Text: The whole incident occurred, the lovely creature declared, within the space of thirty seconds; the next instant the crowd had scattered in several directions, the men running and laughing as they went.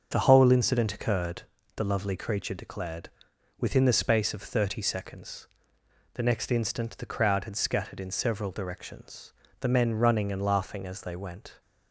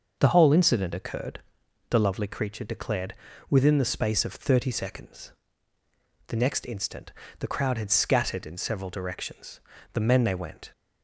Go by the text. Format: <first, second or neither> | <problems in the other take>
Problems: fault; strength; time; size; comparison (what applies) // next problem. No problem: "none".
first | starts louder than the rest; noticeable; until 1.2 s; 6 dB; also in the first // pauses between "instant" and "the"; slight; at 7.1 s; 0.26 s long // skips "running and laughing as"; at 10.2 s